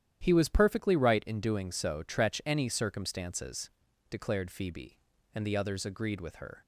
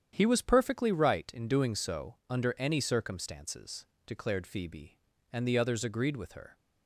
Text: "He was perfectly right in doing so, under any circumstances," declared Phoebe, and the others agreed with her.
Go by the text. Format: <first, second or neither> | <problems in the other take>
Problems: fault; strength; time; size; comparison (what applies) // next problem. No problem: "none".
second | starts louder than the rest; strong; until 1.2 s; 10.5 dB; strong in the second // says "tretch" for "under"; at 2.0 s